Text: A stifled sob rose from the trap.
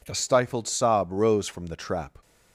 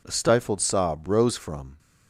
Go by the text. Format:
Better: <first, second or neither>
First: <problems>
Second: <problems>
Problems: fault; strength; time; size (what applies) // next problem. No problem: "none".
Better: first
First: none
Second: stops before "the trap"; at 1.7 s